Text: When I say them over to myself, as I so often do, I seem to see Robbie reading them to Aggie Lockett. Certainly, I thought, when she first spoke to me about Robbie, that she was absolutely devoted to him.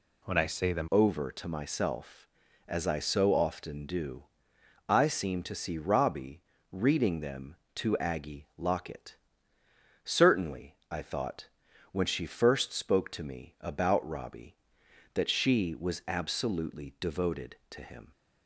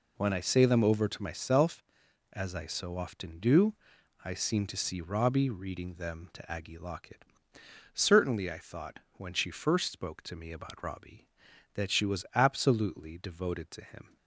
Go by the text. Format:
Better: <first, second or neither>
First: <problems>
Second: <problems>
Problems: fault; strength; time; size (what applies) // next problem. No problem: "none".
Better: second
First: changes voice at "over"; from 0.9 s on; 17.2 s long // pauses between "Robbie" and "reading"; slight; at 6.4 s; 0.30 s long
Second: none